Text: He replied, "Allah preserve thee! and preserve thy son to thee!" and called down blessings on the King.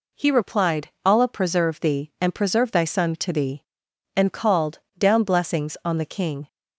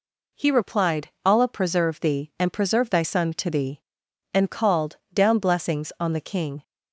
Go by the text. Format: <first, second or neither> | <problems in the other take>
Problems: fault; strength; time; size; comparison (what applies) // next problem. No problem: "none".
neither | pauses between "called" and "down"; slight; the same in both